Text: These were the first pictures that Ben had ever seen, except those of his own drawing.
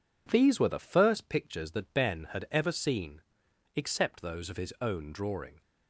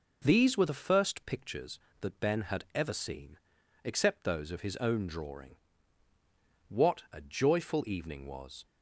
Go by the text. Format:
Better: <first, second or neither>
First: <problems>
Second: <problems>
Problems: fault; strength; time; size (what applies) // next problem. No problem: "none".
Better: first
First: none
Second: goes on to say "What a joyful evening was"; strong; from 6.6 s on; 1.9 s long